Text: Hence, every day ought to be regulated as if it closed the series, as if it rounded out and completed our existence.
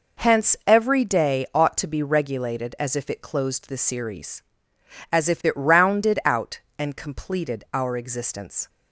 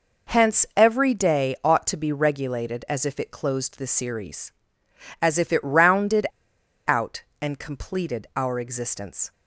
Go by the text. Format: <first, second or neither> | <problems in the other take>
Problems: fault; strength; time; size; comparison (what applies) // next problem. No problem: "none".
first | pauses between "rounded" and "out"; noticeable; at 6.2 s; 0.63 s long